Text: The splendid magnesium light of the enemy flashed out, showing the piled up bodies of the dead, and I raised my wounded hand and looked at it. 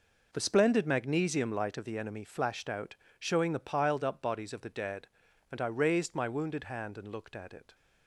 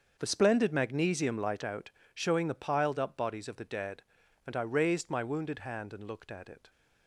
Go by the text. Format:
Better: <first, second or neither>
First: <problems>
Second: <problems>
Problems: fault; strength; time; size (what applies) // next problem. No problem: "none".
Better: first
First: none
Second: starts louder than the rest; until 1.2 s; 6.5 dB // skips "of the enemy flashed"; at 1.6 s